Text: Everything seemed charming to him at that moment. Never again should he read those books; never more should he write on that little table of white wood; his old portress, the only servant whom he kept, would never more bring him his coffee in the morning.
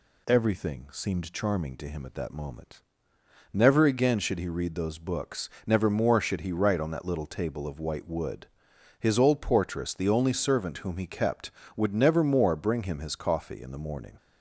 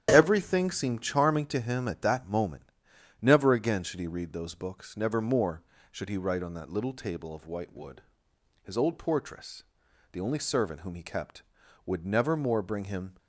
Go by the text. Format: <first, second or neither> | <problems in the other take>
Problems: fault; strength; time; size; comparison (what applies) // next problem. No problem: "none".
first | starts louder than the rest; strong; until 1.1 s; 10 dB // stops before "his coffee in the morning"; at 13.1 s